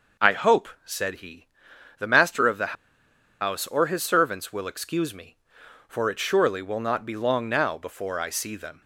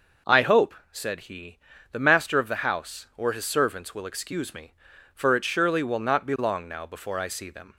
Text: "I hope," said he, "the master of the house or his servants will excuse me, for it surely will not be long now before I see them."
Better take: second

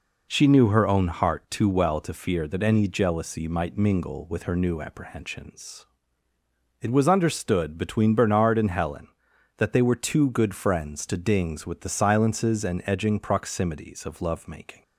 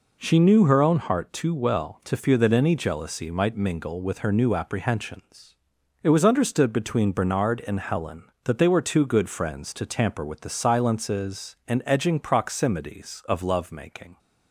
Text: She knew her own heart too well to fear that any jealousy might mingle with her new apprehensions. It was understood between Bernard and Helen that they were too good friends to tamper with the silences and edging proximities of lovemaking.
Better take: second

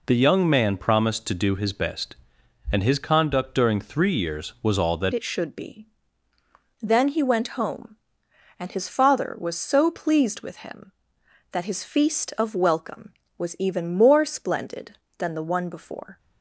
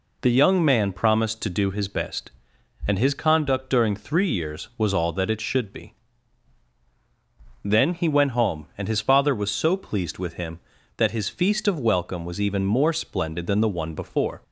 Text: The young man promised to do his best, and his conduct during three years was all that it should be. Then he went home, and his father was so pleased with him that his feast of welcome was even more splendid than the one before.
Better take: second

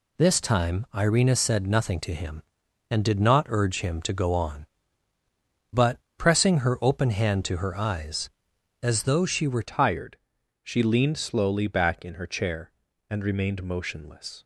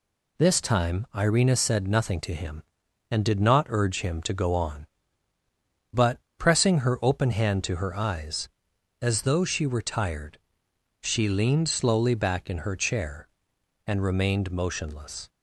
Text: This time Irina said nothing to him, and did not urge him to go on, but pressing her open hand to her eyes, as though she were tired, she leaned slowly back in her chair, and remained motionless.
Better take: second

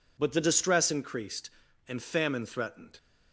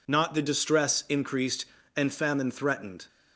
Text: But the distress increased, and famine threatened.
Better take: first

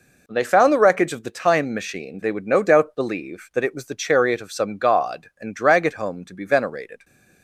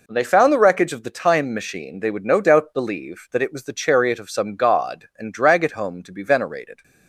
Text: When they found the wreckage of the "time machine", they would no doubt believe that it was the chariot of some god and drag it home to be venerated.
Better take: neither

